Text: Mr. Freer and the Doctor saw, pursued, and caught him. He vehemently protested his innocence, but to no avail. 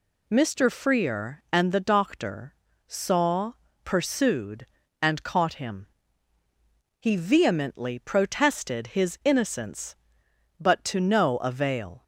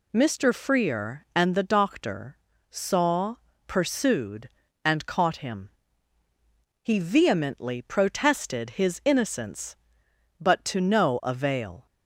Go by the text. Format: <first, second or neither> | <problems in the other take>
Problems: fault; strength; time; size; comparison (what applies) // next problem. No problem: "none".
neither | pauses between "Doctor" and "saw"; slight; the same in both